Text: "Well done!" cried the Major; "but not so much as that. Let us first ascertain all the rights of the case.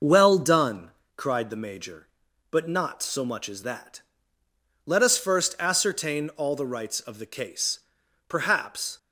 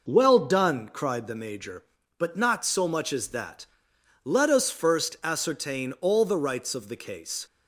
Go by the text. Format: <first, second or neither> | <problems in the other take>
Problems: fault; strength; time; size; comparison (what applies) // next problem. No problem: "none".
second | goes on to say "Perhaps"; noticeable; from 8.2 s on; 0.70 s long